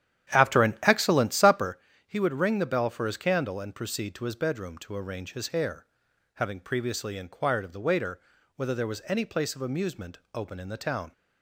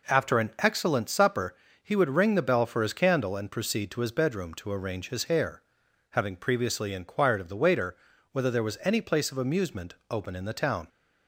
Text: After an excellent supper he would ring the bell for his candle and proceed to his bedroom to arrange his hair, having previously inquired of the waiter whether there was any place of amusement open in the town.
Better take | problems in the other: second | starts louder than the rest; strong; until 1.7 s; 10.5 dB // pauses between "supper" and "he"; slight; at 1.7 s; 0.28 s long; slight in the second // pauses between "waiter" and "whether"; slight; at 8.2 s; 0.36 s long; slight in the second // pauses between "amusement" and "open"; slight; at 10.1 s; 0.16 s long; slight in the second

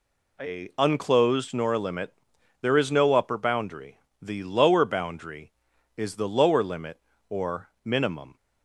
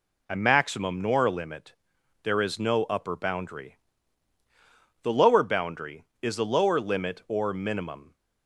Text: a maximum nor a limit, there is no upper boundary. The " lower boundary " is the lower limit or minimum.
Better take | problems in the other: second | says "unclosed" for "maximum"; at 0.7 s // pauses between "or" and "minimum"; slight; at 7.6 s; 0.16 s long

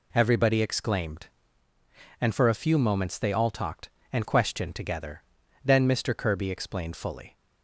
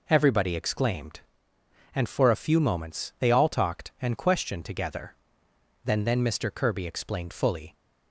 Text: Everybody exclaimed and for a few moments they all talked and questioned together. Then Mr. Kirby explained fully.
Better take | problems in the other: first | says "Then" twice; at 6.0 s

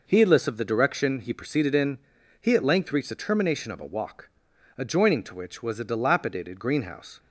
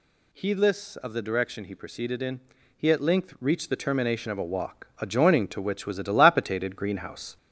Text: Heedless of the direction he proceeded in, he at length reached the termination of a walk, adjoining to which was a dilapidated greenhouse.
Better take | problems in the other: first | gets louder; throughout; 3.5 dB

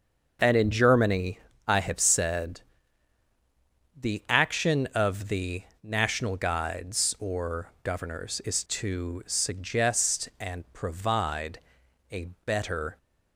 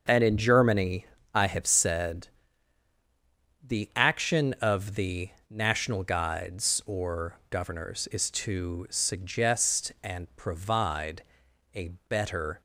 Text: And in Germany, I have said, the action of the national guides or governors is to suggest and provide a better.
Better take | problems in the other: neither | starts louder than the rest; the same in both // pauses between "the" and "national"; slight; the same in both // pauses between "provide" and "a"; noticeable; the same in both // pauses between "a" and "better"; slight; the same in both

